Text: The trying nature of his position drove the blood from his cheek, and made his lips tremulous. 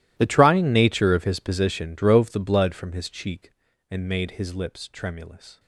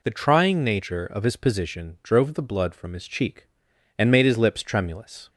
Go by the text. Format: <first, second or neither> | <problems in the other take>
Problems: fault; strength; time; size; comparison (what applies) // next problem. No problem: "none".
second | gets quieter; strong; throughout; 21.5 dB